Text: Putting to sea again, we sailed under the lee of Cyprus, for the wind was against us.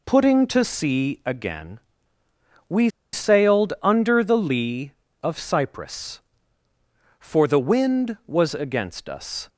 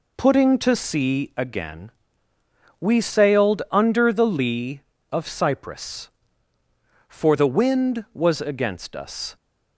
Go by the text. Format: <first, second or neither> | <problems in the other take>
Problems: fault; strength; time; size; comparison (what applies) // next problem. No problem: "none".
second | pauses between "we" and "sailed"; slight; at 2.8 s; 0.23 s long